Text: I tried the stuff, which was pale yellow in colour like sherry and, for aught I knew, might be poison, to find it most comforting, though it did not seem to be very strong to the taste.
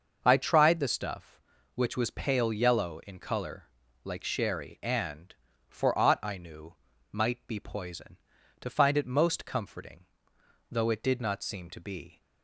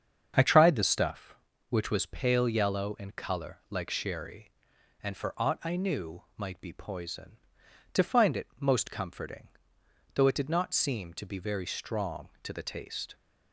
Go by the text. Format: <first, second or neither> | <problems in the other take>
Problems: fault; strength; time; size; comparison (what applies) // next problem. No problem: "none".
second | starts louder than the rest; noticeable; until 1.2 s; 6 dB; strong in the second // pauses between "colour" and "like"; at 3.6 s; 0.40 s long // stops before "very strong to the taste"; at 12.2 s